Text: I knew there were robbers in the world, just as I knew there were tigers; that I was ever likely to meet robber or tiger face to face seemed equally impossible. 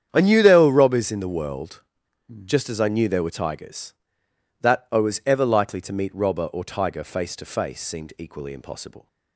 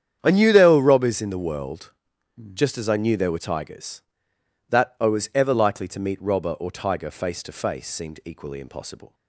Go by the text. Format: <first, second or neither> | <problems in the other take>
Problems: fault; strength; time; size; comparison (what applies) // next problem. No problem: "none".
neither | starts louder than the rest; strong; the same in both